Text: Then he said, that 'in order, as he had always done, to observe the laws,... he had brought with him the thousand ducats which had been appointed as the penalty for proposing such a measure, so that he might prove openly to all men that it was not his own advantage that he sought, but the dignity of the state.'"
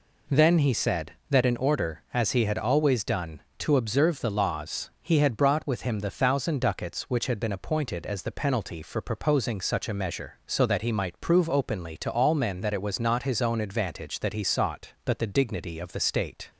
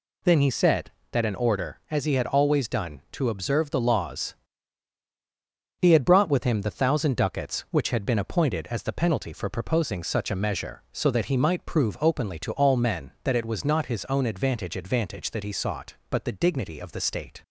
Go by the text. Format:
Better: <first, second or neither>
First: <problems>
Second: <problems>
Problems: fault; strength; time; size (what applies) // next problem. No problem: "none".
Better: first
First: none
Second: says "advantage" twice; at 14.7 s